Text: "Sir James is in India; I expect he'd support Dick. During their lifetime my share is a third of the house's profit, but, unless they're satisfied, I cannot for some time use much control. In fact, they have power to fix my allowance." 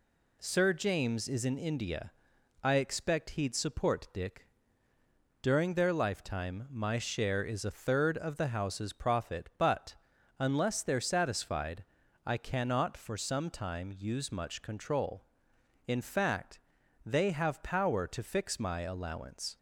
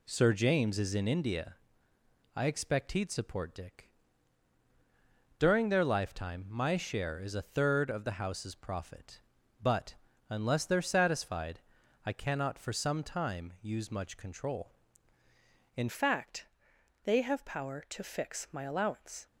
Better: first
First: none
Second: changes voice at "fact"; from 15.8 s on; 3.4 s long

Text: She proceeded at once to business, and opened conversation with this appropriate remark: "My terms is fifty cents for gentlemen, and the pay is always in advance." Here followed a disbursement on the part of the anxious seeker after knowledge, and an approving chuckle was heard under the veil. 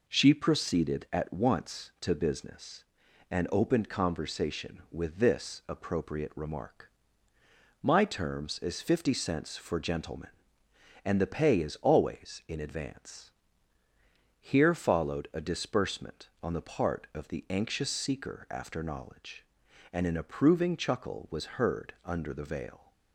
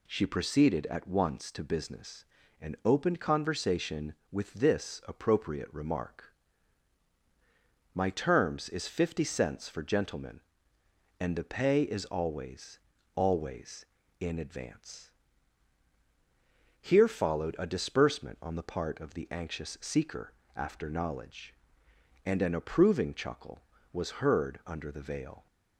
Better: first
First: none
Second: says "always" twice; at 13.1 s // pauses between "seeker" and "after"; slight; at 20.3 s; 0.20 s long

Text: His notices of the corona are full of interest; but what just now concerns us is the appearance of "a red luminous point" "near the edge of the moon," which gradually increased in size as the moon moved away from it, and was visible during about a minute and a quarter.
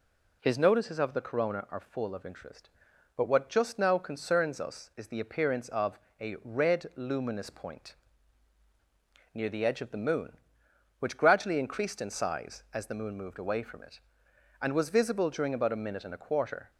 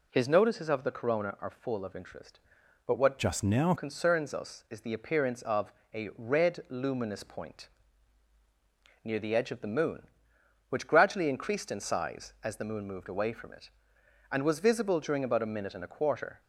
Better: first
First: pauses between "of" and "a"; slight; at 5.9 s; 0.20 s long // pauses between "point" and "near"; strong; at 7.9 s; 1.3 s long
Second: changes voice from "just" to "now"; from 3.1 to 3.7 s; 0.6 s long // pauses between "of" and "a"; slight; at 5.7 s; 0.20 s long // pauses between "point" and "near"; strong; at 7.6 s; 1.3 s long

